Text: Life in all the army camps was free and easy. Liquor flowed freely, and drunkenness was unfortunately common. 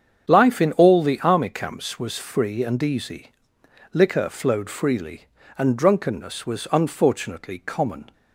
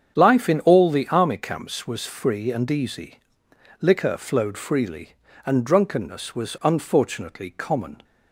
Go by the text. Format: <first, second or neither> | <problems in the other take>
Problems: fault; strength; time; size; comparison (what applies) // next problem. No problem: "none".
neither | starts louder than the rest; strong; the same in both